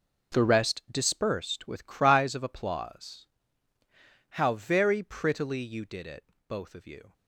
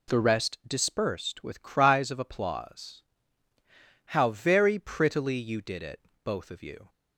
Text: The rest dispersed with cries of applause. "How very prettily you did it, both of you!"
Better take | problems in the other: second | gets quieter; strong; throughout; 12.5 dB

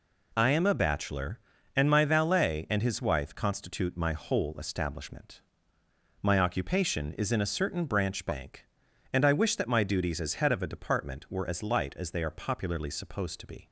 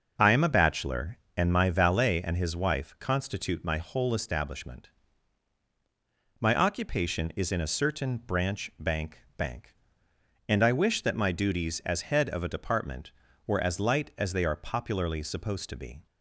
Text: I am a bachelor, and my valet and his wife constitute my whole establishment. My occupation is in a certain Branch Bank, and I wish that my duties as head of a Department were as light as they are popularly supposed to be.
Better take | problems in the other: first | starts louder than the rest; noticeable; until 1.1 s; 6 dB // says "Bank" twice; at 9.3 s

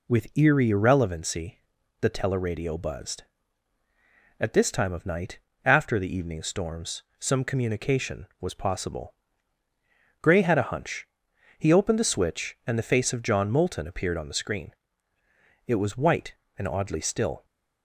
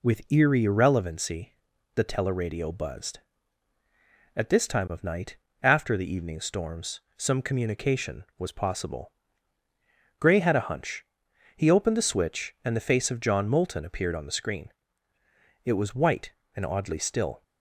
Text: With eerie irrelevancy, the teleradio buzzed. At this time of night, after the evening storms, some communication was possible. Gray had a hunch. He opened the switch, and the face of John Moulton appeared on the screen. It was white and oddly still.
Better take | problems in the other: neither | none

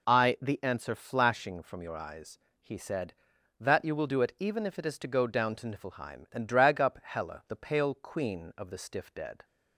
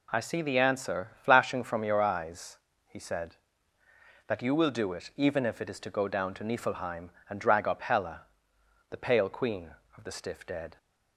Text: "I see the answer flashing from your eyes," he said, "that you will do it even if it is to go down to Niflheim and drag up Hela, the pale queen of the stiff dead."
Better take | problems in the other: second | skips "see"; at 0.3 s

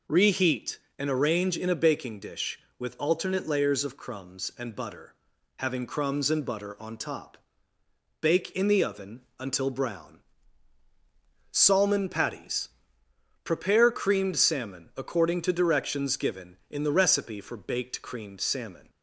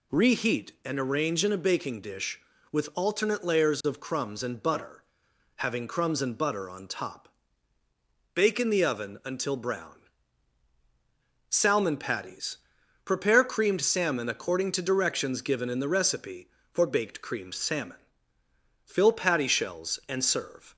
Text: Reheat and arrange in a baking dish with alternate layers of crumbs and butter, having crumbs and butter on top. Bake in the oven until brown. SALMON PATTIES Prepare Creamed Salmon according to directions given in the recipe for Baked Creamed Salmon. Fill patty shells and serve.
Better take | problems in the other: second | pauses between "PATTIES" and "Prepare"; noticeable; at 12.6 s; 0.74 s long; noticeable in the second // stops before "Fill patty shells and serve"; at 18.8 s

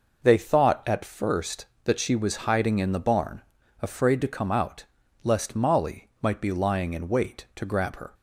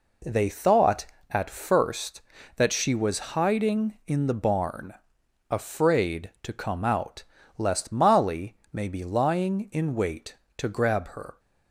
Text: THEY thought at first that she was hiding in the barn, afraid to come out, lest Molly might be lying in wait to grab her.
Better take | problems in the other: first | says "may" for "might"; at 8.7 s

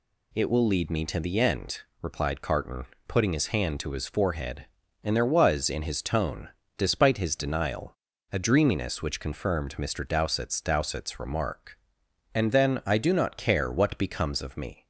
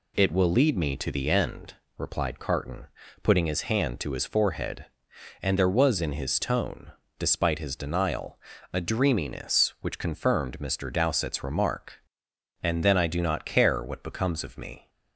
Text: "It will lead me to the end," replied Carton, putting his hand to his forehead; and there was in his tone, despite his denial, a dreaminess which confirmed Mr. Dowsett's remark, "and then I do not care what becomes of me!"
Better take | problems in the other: second | says "Dowsett's" twice; at 10.6 s

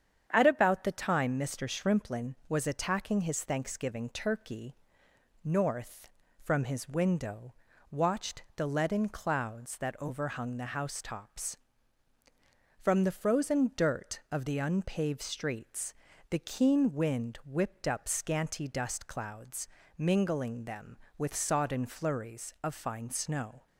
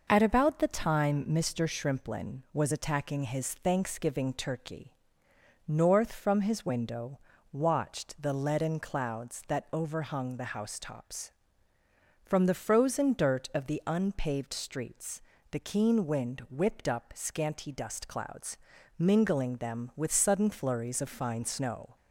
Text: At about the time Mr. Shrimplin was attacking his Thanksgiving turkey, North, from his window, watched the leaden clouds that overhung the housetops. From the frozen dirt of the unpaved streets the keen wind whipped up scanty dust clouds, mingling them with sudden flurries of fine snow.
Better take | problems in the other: second | starts louder than the rest; strong; until 1.3 s; 8 dB // pauses between "streets" and "the"; slight; at 15.9 s; 0.36 s long; slight in the second // says "sodden" for "sudden"; at 21.3 s

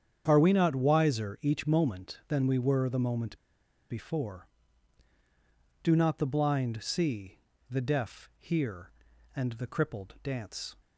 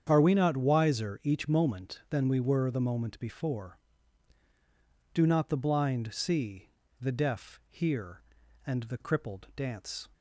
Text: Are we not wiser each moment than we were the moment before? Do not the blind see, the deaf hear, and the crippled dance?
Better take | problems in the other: second | starts louder than the rest; strong; until 1.2 s; 8 dB; strong in the second // pauses between "moment" and "before"; noticeable; at 3.3 s; 0.51 s long

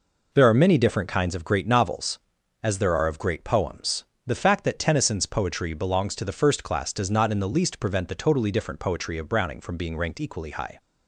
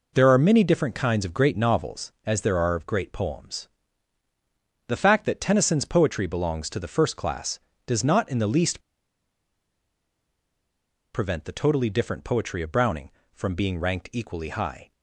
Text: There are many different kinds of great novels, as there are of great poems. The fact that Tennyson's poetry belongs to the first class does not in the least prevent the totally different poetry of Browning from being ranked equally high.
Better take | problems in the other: first | pauses between "least" and "prevent"; strong; at 8.7 s; 2.3 s long

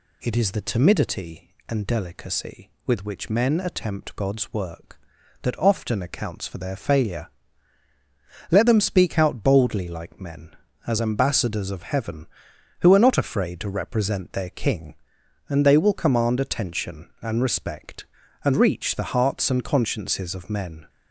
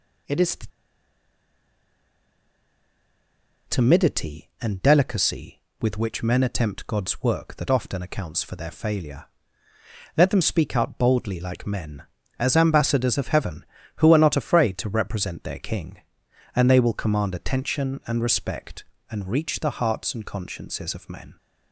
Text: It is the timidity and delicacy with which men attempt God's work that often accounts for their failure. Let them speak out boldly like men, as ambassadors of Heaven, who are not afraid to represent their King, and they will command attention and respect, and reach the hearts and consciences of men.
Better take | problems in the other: first | pauses between "the" and "timidity"; strong; at 0.6 s; 3.0 s long

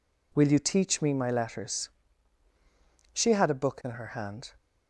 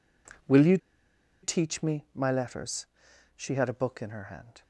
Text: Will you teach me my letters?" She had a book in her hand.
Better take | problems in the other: first | pauses between "you" and "teach"; noticeable; at 0.7 s; 0.65 s long

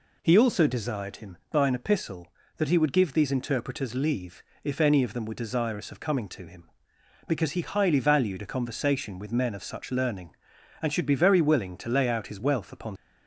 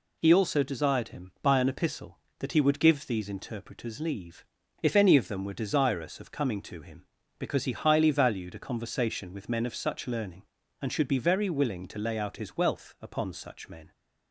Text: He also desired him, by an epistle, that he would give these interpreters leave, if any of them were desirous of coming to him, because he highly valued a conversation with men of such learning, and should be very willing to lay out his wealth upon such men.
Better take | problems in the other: second | stops before "such men"; at 12.9 s

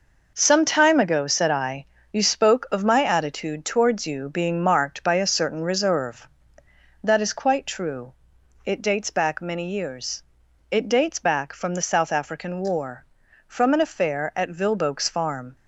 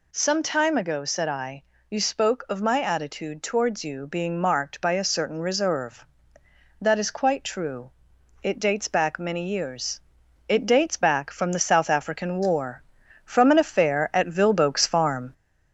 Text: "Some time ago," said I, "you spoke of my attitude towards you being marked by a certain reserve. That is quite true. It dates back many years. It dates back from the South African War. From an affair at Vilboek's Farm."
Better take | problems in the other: first | gets louder; slight; throughout; 2 dB

